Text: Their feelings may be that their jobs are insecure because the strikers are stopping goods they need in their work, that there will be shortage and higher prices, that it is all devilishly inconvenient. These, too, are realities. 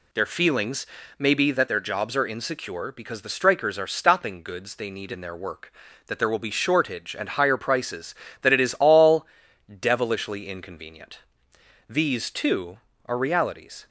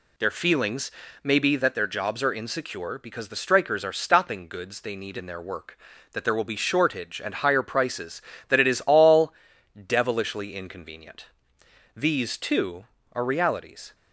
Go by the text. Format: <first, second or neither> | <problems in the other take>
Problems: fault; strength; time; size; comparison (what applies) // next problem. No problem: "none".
neither | pauses between "feelings" and "may"; slight; the same in both // pauses between "all" and "devilishly"; the same in both